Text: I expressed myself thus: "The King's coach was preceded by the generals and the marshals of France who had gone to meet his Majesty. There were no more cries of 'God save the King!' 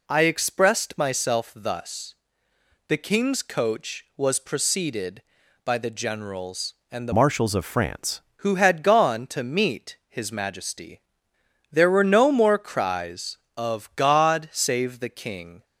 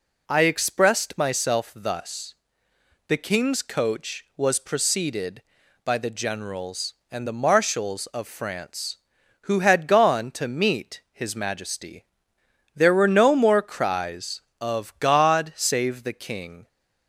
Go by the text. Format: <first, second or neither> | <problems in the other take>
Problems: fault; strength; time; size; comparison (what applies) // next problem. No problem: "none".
second | changes voice from "marshals" to "France"; from 7.1 to 8.2 s; 1.1 s long